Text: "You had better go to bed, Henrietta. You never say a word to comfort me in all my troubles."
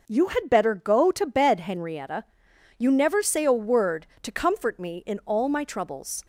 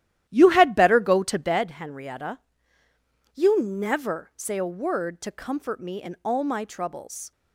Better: first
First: none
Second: starts louder than the rest; strong; until 1.7 s; 12.5 dB

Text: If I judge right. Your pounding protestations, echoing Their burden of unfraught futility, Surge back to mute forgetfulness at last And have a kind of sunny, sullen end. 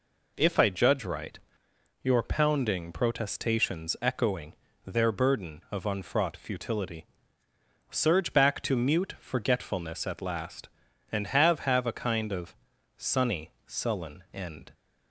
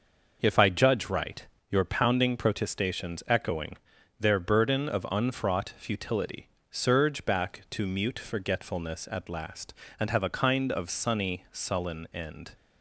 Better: second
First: pauses between "echoing" and "Their"; slight; at 4.5 s; 0.32 s long // says "have" twice; at 11.5 s // pauses between "of" and "sunny"; at 12.5 s; 0.44 s long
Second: pauses between "echoing" and "Their"; at 3.7 s; 0.42 s long

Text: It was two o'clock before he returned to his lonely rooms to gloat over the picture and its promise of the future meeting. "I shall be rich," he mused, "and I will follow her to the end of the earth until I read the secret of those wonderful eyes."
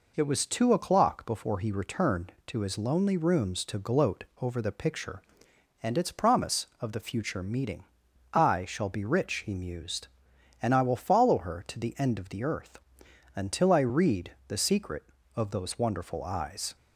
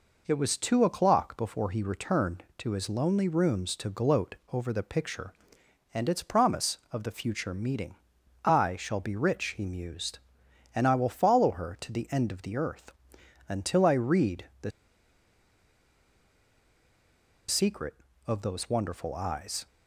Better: first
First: pauses between "earth" and "until"; noticeable; at 12.7 s; 0.56 s long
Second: pauses between "earth" and "until"; noticeable; at 12.9 s; 0.56 s long // pauses between "the" and "secret"; strong; at 14.7 s; 2.7 s long

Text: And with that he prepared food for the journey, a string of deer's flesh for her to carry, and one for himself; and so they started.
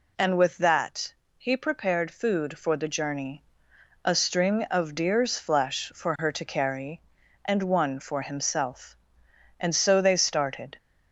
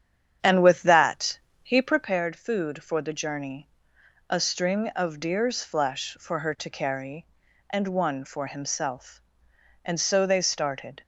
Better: first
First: pauses between "that" and "he"; slight; at 1.1 s; 0.24 s long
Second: starts louder than the rest; strong; until 2.2 s; 8.5 dB // pauses between "that" and "he"; slight; at 1.3 s; 0.24 s long

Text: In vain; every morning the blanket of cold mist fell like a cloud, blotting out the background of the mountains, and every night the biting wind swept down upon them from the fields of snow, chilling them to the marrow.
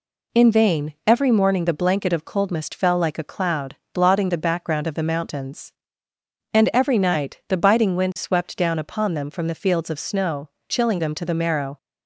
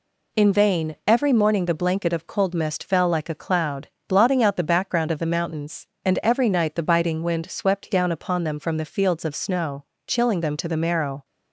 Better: second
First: skips "out"; at 4.2 s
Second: none

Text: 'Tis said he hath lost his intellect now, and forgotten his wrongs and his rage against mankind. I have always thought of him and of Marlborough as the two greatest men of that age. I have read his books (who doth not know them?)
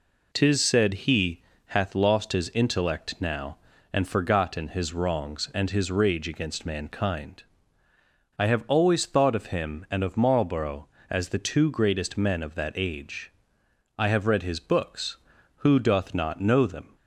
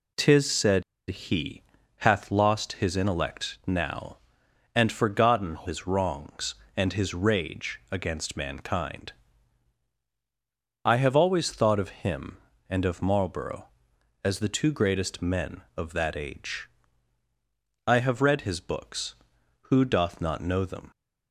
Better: first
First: pauses between "he" and "hath"; slight; at 1.4 s; 0.26 s long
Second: pauses between "said" and "he"; slight; at 0.8 s; 0.25 s long // pauses between "he" and "hath"; slight; at 1.6 s; 0.36 s long

